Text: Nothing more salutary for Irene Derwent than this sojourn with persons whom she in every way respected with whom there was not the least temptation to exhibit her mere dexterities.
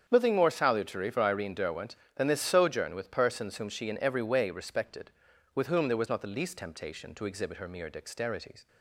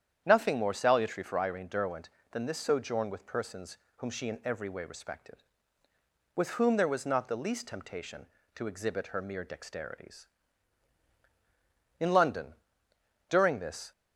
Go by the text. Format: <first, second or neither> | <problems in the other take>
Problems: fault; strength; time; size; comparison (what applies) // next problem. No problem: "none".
first | starts louder than the rest; strong; until 1.2 s; 9 dB; strong in the first // pauses between "persons" and "whom"; slight; at 3.7 s; 0.20 s long // goes on to say "In London during this"; strong; from 11.9 s on; 1.9 s long